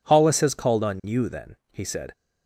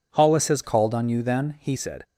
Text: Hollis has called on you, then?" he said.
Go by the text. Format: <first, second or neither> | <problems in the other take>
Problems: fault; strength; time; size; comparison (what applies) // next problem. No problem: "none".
first | changes voice from "called" to "he"; from 0.6 to 1.7 s; 1.1 s long